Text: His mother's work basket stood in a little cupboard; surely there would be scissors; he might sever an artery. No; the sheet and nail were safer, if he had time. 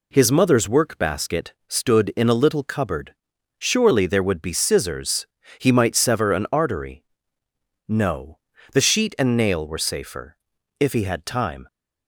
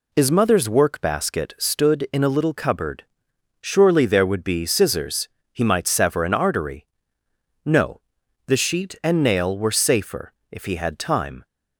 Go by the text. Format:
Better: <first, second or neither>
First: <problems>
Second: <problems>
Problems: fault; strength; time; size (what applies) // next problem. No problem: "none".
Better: neither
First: none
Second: none